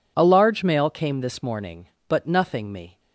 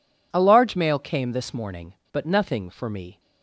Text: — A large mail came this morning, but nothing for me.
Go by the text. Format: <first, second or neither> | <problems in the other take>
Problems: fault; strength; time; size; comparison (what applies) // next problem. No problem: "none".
second | skips "for"; at 2.7 s